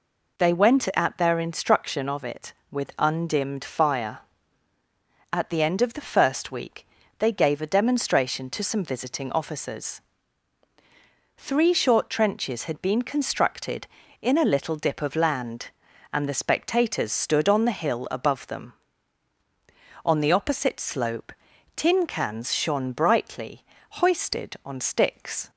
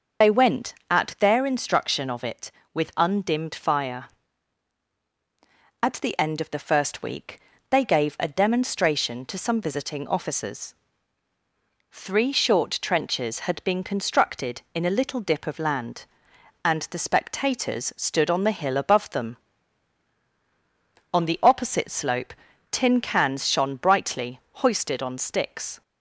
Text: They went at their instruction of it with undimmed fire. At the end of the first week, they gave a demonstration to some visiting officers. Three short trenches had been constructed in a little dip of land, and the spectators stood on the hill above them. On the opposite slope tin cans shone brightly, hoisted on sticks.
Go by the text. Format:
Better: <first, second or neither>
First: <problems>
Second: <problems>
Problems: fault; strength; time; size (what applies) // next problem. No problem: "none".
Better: first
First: pauses between "slope" and "tin"; at 21.3 s; 0.44 s long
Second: loses the start of "They"; at 0.2 s; 50 ms // pauses between "slope" and "tin"; slight; at 22.3 s; 0.36 s long